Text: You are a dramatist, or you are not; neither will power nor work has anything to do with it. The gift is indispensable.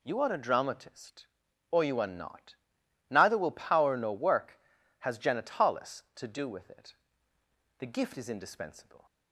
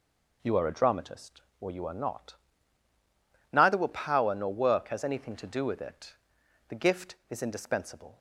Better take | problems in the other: second | says "genitalis" for "anything"; at 5.1 s

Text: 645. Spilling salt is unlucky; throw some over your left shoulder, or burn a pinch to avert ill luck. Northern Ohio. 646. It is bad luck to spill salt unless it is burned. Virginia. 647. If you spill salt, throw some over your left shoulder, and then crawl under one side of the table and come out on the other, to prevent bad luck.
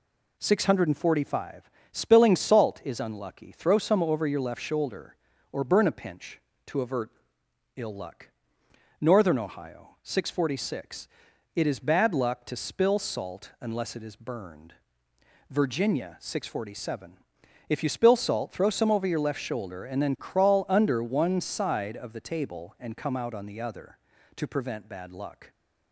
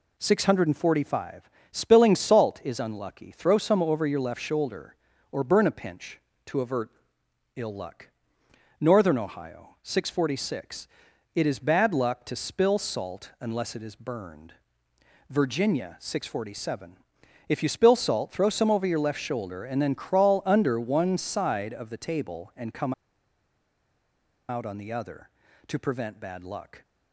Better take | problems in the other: first | pauses between "avert" and "ill"; noticeable; at 6.8 s; 0.66 s long; noticeable in the first // pauses between "come" and "out"; strong; at 22.9 s; 1.5 s long

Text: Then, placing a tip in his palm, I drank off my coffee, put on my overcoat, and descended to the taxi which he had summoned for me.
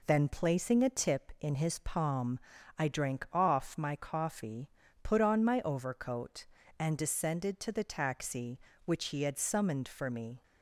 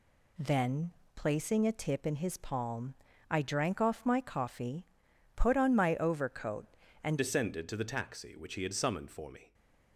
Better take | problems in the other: first | changes voice at "descended"; from 7.1 s on; 2.4 s long // stays silent after the last word; slight; from 9.4 s on; 0.5 s long

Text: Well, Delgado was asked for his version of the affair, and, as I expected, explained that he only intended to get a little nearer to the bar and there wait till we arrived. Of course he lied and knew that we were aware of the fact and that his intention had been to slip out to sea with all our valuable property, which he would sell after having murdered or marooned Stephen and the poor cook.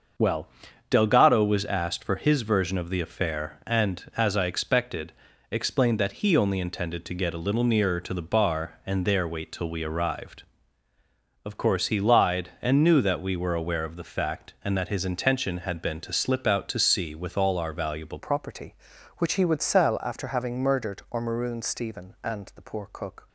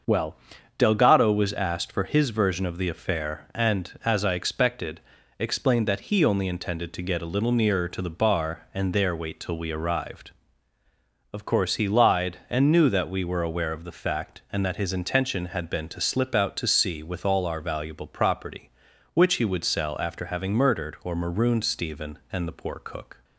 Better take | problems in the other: second | starts louder than the rest; until 1.6 s; 6.5 dB; also in the second // changes voice at "property"; from 18.1 s on; 5.1 s long

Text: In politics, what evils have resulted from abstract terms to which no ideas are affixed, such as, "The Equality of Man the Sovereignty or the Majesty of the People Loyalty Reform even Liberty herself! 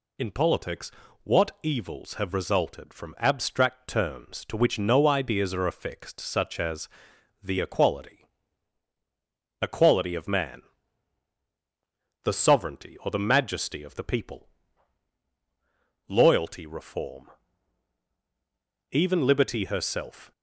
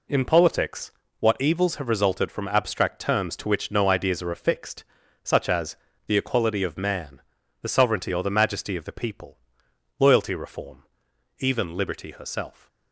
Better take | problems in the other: second | says "Equality" twice; at 9.6 s // pauses between "Man" and "the"; strong; at 10.6 s; 1.6 s long; also in the second // pauses between "People" and "Loyalty"; strong; at 14.4 s; 1.6 s long; noticeable in the second // pauses between "Reform" and "even"; strong; at 17.2 s; 1.6 s long; noticeable in the second

